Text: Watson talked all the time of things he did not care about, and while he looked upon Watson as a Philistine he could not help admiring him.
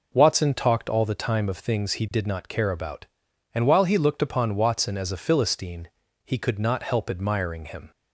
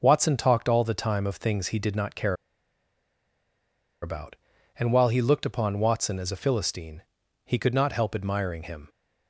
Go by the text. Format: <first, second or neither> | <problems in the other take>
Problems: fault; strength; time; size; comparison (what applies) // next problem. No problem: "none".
first | starts louder than the rest; until 1.0 s; 6 dB // pauses between "care" and "about"; strong; at 2.3 s; 1.6 s long // pauses between "Philistine" and "he"; at 7.0 s; 0.42 s long; slight in the first